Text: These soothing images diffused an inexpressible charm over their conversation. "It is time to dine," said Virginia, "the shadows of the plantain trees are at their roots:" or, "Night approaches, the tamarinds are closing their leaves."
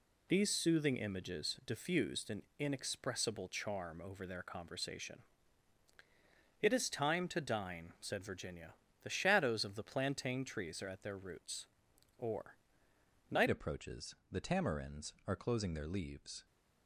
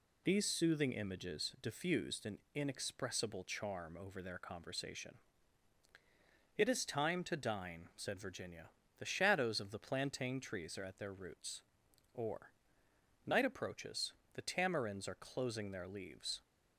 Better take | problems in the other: second | changes voice at "approaches"; from 13.4 s on; 3.0 s long

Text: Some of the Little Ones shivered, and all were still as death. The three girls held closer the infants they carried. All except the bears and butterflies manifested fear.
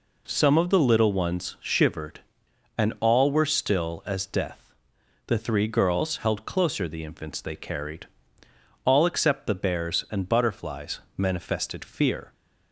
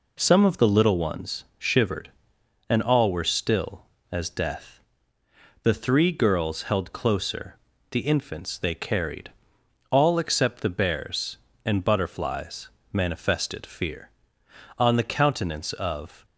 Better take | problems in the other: first | pauses between "Ones" and "shivered"; slight; at 1.4 s; 0.16 s long // pauses between "closer" and "the"; slight; at 7.5 s; 0.34 s long // pauses between "butterflies" and "manifested"; slight; at 12.6 s; 0.24 s long; slight in the first // goes on to say "On the countenance of"; from 14.7 s on; 1.4 s long

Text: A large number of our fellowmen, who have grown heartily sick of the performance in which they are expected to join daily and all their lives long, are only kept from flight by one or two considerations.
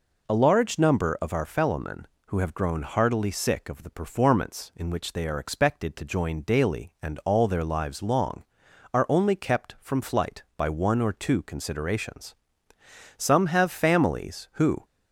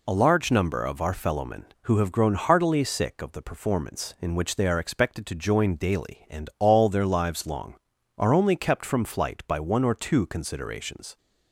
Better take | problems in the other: second | goes on to say "Some have families who"; from 13.2 s on; 1.6 s long

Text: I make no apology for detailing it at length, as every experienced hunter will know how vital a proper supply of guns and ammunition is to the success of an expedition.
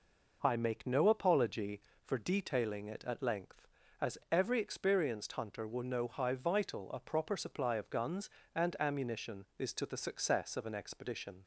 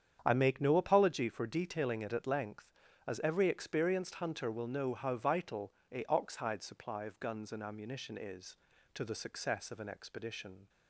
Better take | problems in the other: first | starts louder than the rest; strong; until 1.2 s; 8.5 dB // pauses between "vital" and "a"; slight; at 5.7 s; 0.22 s long // says "oxhide" for "proper"; at 6.0 s

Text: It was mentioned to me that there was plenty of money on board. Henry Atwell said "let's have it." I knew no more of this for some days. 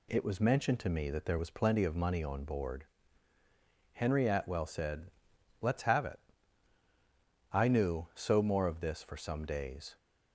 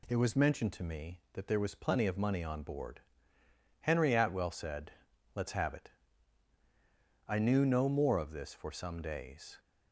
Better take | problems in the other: second | pauses between "said" and "let's"; noticeable; at 5.1 s; 0.50 s long; also in the second // says "so" for "no"; at 8.1 s

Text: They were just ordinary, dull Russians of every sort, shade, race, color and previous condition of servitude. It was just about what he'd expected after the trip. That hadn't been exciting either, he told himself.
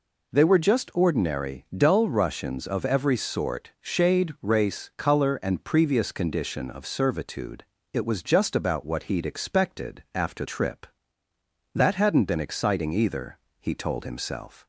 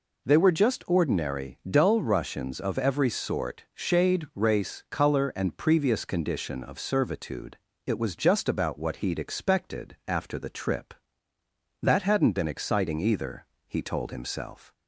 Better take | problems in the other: second | skips "the"; at 10.4 s

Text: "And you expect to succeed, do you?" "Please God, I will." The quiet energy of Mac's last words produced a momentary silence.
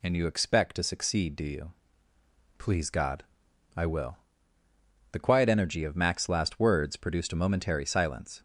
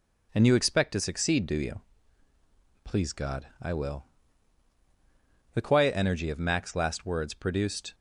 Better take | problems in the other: first | stops before "a momentary silence"; at 7.9 s

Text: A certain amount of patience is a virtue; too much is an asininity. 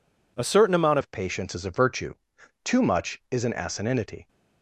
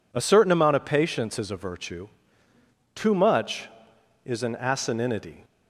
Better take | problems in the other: second | changes voice at "of"; from 1.0 s on; 3.2 s long

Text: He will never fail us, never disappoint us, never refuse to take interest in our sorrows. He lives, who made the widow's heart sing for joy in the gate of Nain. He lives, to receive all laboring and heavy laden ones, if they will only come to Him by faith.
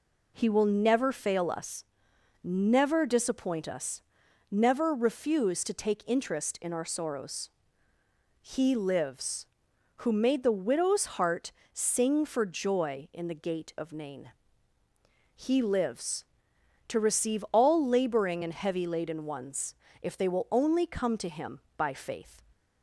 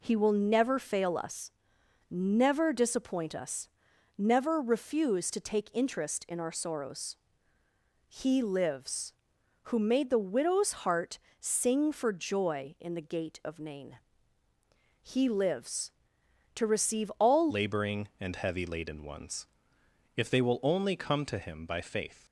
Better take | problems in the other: first | pauses between "heart" and "sing"; slight; at 11.1 s; 0.20 s long; slight in the first // changes voice at "laboring"; from 17.4 s on; 4.8 s long

